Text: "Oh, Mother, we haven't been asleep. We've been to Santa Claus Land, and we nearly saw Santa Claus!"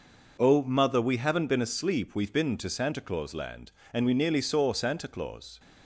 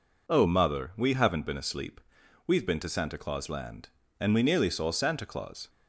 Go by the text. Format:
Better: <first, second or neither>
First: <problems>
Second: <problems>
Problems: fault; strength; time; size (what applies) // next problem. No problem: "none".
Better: neither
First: none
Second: none